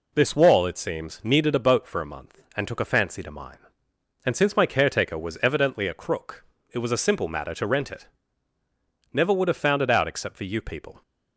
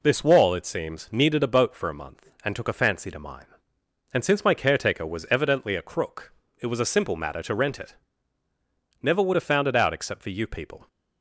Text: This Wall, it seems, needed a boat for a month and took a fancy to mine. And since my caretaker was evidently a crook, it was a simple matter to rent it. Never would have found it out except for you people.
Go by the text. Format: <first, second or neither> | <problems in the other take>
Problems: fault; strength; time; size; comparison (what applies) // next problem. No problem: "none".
neither | none